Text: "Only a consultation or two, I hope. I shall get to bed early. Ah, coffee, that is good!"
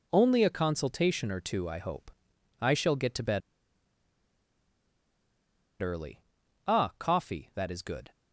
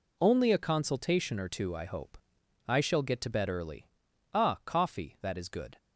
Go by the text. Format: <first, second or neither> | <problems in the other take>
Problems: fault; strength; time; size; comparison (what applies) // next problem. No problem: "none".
second | pauses between "bed" and "early"; strong; at 3.4 s; 2.4 s long